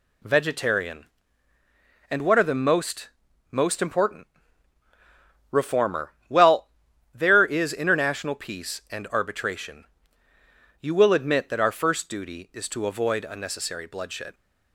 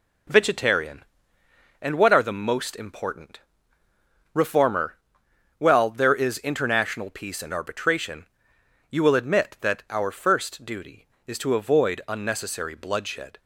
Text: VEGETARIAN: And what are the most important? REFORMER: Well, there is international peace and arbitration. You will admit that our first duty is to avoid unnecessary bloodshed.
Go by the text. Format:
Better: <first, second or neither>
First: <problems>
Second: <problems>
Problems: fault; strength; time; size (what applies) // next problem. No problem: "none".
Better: second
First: says "most" twice; at 3.4 s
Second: none